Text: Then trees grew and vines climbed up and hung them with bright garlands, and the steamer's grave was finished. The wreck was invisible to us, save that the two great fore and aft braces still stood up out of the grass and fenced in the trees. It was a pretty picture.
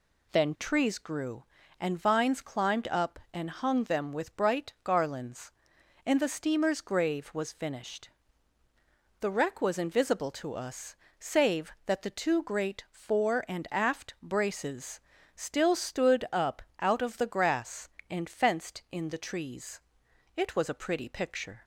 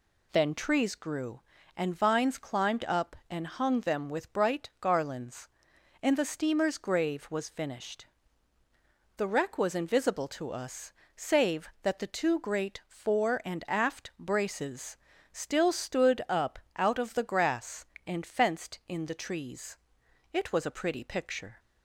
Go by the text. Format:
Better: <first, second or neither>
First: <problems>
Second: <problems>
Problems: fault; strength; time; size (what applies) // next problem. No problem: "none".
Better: neither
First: pauses between "braces" and "still"; slight; at 15.0 s; 0.34 s long // pauses between "up" and "out"; slight; at 16.6 s; 0.16 s long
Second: pauses between "braces" and "still"; slight; at 14.9 s; 0.34 s long // pauses between "up" and "out"; slight; at 16.5 s; 0.16 s long